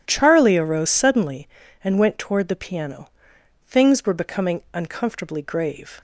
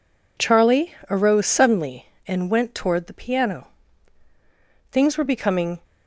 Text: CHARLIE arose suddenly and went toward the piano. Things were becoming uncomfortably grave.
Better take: first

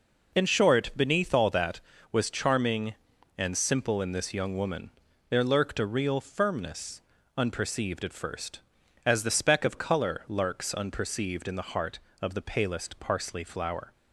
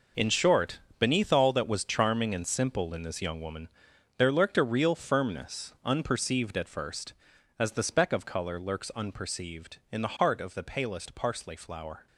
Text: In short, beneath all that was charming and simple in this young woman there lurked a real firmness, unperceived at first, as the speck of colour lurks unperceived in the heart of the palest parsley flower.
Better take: first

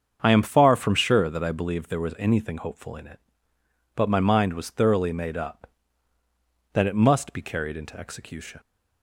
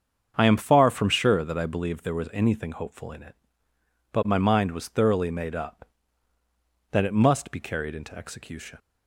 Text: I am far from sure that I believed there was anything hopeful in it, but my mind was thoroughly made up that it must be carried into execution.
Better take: neither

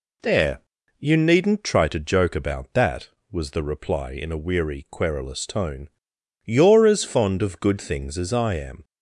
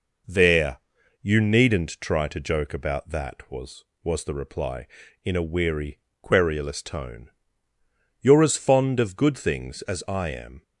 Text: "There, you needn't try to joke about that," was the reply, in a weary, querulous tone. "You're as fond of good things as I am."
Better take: first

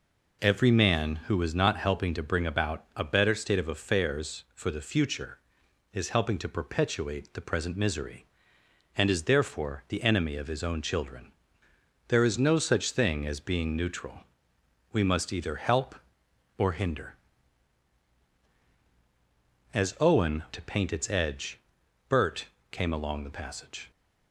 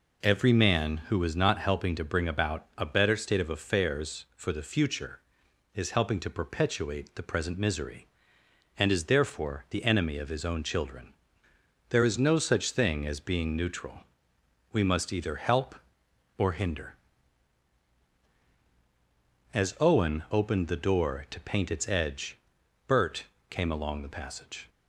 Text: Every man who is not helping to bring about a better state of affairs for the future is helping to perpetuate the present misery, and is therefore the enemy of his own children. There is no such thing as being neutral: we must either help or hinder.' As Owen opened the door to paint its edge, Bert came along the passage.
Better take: second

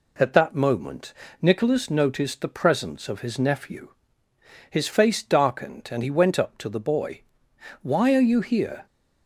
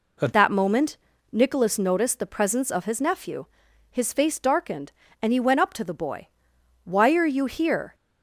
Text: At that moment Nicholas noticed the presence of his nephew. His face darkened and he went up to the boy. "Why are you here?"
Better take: first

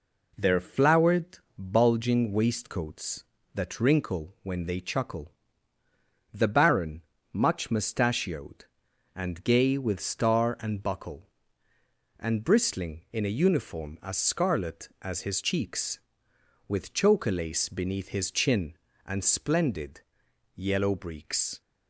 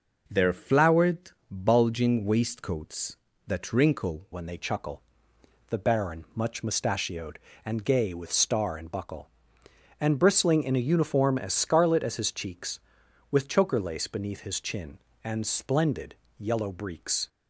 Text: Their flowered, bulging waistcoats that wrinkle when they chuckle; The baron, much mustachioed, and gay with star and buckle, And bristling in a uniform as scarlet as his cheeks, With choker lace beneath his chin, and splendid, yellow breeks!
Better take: first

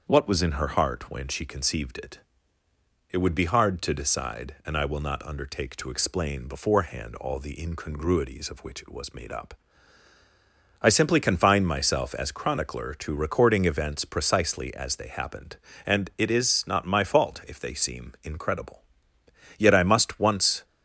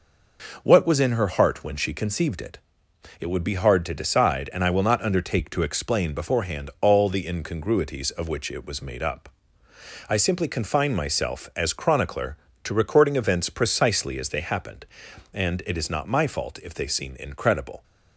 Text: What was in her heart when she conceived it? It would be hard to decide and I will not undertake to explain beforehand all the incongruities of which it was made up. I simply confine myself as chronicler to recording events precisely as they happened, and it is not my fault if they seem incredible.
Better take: second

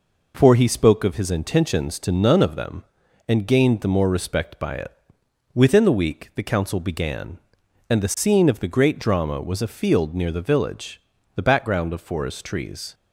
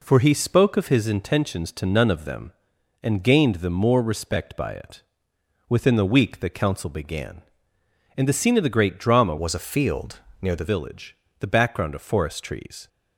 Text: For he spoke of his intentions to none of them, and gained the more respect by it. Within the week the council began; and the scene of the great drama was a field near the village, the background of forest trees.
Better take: first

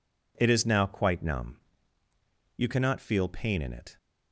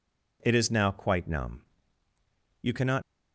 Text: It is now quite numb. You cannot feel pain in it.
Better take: first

